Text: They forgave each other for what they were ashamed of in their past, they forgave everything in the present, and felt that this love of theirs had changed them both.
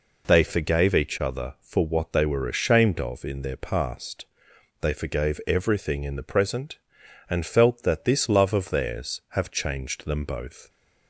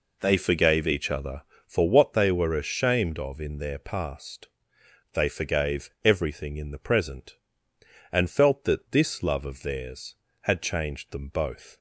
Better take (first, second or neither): second